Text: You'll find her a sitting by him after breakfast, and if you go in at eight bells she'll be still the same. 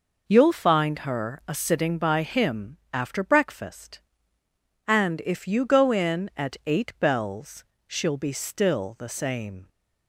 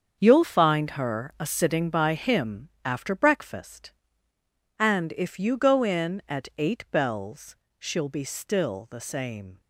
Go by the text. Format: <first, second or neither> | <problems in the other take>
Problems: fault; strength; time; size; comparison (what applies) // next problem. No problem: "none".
first | gets quieter; strong; throughout; 9.5 dB // pauses between "bells" and "she'll"; slight; at 7.5 s; 0.24 s long; slight in the first